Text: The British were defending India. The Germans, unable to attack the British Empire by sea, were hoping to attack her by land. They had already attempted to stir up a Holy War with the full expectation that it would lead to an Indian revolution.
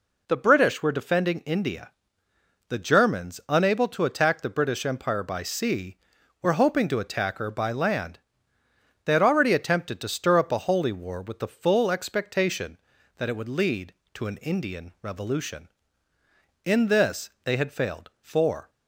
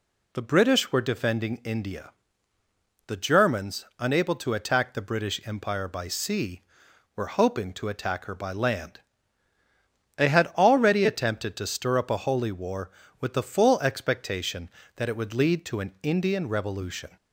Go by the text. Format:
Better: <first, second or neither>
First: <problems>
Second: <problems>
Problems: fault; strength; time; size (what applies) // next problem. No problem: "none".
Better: second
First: goes on to say "In this they had failed for"; strong; from 16.6 s on; 2.0 s long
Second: none